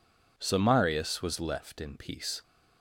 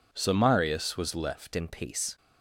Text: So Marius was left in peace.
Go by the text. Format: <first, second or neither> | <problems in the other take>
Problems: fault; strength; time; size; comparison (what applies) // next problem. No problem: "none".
first | changes voice at "in"; from 1.5 s on; 0.6 s long